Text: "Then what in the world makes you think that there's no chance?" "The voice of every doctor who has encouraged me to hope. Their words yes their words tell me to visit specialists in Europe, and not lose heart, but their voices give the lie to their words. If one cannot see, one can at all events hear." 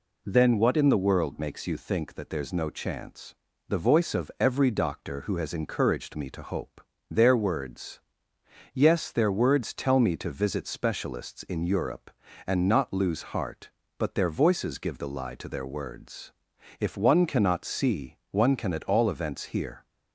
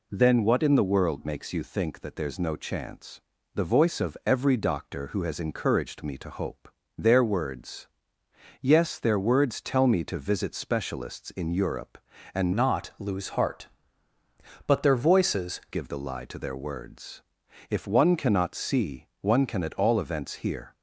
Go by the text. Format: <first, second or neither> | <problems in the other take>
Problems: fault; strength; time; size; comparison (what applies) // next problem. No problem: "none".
first | pauses between "words" and "yes"; noticeable; at 7.8 s; 0.74 s long; noticeable in the first // changes voice from "not" to "voices"; from 12.5 to 15.5 s; 3.0 s long